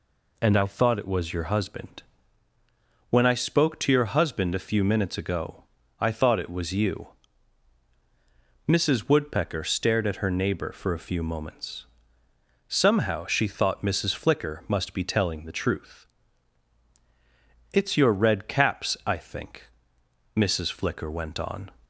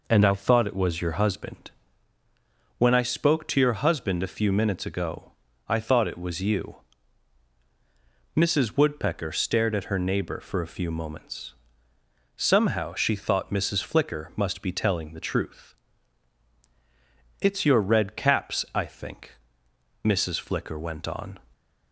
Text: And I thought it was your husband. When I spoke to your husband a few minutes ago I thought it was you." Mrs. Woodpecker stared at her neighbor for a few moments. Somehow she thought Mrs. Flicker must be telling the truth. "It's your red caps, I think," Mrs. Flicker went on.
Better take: first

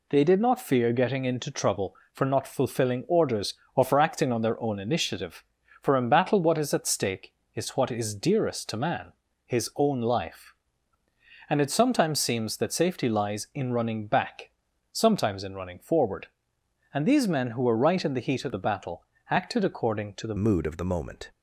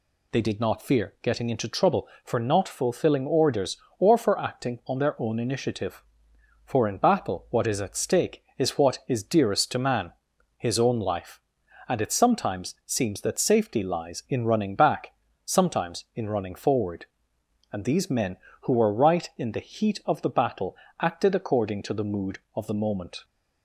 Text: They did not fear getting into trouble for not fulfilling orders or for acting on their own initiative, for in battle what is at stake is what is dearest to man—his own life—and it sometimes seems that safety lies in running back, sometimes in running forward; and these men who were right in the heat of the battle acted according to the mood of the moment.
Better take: second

